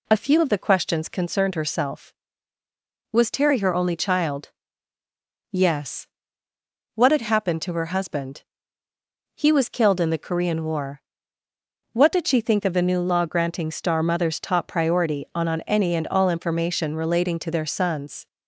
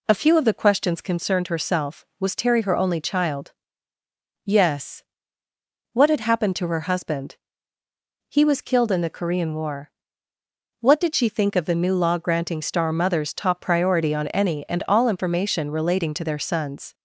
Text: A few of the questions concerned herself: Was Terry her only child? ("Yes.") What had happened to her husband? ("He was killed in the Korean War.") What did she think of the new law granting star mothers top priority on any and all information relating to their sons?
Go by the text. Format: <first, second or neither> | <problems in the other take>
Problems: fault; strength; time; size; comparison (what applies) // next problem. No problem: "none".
second | says "on" twice; at 15.4 s